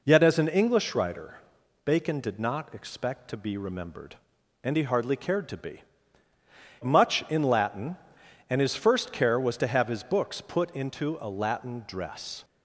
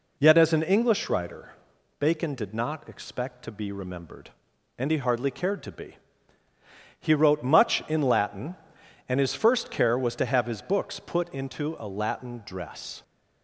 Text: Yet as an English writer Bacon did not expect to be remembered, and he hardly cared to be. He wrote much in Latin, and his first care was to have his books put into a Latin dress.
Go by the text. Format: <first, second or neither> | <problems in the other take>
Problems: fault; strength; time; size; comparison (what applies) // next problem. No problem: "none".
second | pauses between "writer" and "Bacon"; noticeable; at 1.3 s; 0.46 s long; noticeable in the second // skips "He wrote"; at 6.3 s